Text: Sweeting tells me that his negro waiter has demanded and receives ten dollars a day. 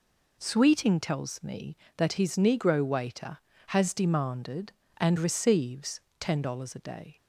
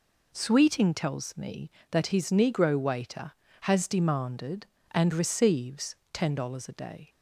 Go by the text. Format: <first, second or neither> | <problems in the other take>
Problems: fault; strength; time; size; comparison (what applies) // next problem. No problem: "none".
neither | pauses between "receives" and "ten"; slight; the same in both